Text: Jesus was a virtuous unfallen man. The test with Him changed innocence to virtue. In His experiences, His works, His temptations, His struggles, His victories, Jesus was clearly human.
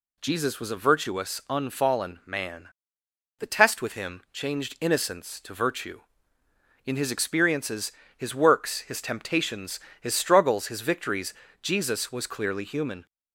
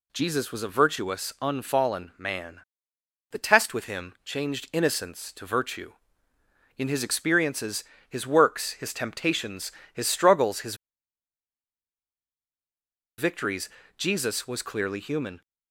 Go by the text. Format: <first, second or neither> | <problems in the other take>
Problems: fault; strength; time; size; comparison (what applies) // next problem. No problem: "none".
first | pauses between "His" and "victories"; strong; at 10.7 s; 2.4 s long